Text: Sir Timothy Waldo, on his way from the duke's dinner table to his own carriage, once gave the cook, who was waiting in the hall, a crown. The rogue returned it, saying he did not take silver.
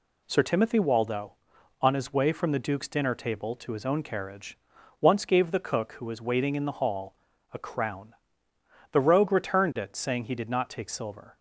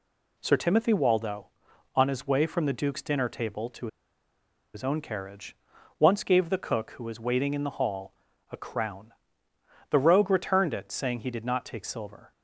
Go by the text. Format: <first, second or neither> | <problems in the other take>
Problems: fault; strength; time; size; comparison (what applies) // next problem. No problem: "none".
first | pauses between "to" and "his"; noticeable; at 3.8 s; 0.87 s long